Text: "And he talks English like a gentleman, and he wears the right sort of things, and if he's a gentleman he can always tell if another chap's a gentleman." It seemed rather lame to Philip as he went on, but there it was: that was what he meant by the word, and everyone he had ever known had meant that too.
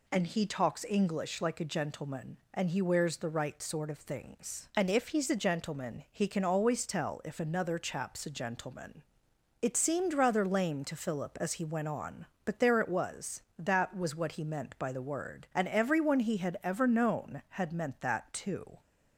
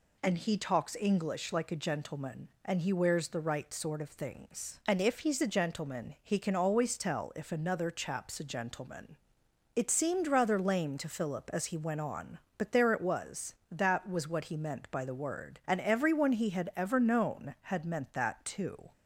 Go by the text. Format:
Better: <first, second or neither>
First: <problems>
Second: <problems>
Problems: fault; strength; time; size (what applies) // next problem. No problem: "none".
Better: neither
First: none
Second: none